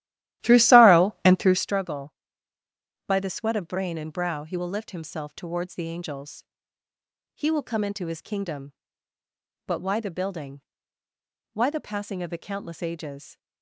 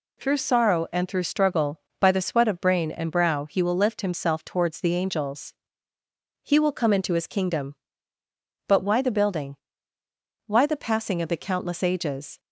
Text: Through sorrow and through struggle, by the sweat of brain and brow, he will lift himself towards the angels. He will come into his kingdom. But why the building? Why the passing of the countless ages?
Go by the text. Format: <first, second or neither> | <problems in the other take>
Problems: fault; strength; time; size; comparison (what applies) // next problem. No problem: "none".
second | starts louder than the rest; strong; until 1.8 s; 14 dB